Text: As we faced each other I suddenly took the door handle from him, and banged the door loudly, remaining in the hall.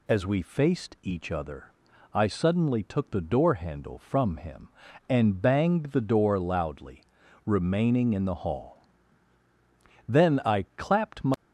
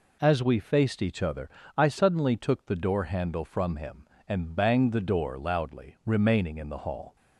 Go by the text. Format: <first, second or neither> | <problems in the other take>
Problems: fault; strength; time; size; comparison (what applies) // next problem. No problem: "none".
second | pauses between "other" and "I"; at 1.7 s; 0.44 s long; slight in the second // goes on to say "Then I clapped my"; noticeable; from 10.0 s on; 1.2 s long